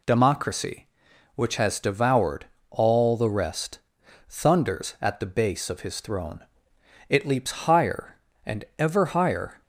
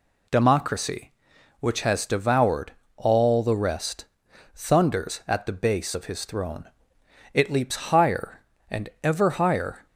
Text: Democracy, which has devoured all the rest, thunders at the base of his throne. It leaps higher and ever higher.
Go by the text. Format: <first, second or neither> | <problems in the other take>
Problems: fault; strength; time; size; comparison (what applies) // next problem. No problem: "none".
neither | pauses between "devoured" and "all"; slight; the same in both